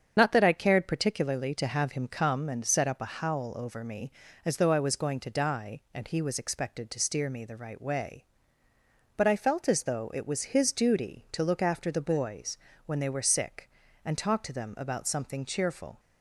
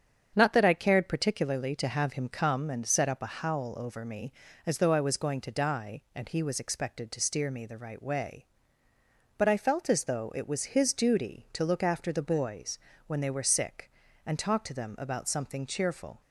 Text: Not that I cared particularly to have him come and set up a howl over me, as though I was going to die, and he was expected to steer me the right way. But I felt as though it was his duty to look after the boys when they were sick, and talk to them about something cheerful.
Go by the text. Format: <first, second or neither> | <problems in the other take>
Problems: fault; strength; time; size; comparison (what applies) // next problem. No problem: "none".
second | loses the start of "Not"; at 0.1 s; 50 ms // starts louder than the rest; strong; until 1.1 s; 7.5 dB; strong in the second // pauses between "boys" and "when"; slight; at 12.5 s; 0.28 s long; slight in the second